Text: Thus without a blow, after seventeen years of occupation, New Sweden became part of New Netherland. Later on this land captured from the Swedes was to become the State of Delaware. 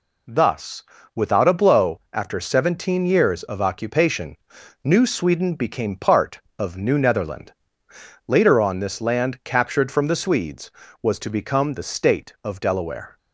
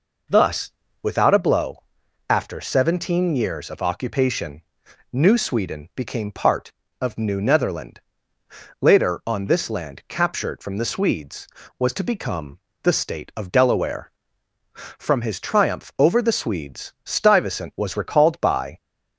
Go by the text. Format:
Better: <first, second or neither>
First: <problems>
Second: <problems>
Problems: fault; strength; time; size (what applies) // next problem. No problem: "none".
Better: first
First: pauses between "Thus" and "without"; slight; at 0.8 s; 0.32 s long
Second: pauses between "Thus" and "without"; slight; at 0.7 s; 0.30 s long // pauses between "become" and "the"; slight; at 12.5 s; 0.26 s long // goes on to say "From his triumph over the Swedes Stuyvesant was recalled by"; strong; from 14.7 s on; 4.0 s long